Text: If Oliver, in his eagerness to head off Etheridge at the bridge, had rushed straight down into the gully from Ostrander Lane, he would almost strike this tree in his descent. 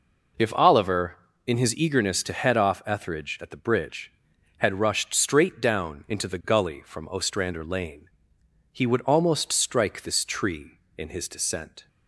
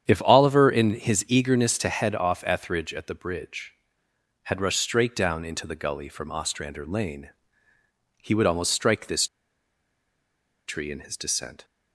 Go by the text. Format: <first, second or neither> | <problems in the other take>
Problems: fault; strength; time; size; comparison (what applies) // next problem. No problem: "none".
first | starts louder than the rest; strong; until 1.1 s; 8.5 dB // pauses between "this" and "tree"; strong; at 9.2 s; 1.4 s long